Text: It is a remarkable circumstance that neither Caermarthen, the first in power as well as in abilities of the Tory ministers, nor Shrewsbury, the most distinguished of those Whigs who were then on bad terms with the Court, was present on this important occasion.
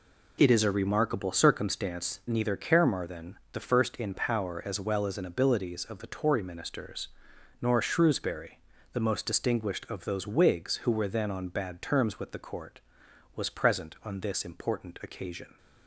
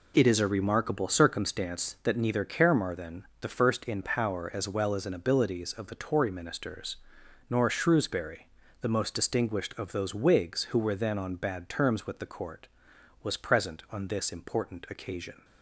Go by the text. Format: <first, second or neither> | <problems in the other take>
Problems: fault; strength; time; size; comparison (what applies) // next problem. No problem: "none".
second | skips "that"; at 2.2 s